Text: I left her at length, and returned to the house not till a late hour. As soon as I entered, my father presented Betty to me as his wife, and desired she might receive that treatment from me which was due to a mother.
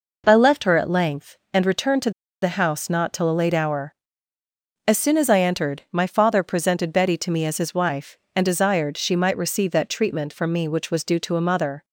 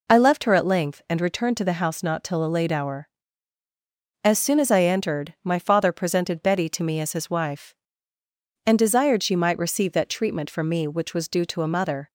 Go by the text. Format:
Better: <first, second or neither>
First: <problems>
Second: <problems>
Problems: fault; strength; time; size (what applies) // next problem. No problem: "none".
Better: second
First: pauses between "to" and "the"; slight; at 2.1 s; 0.31 s long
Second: none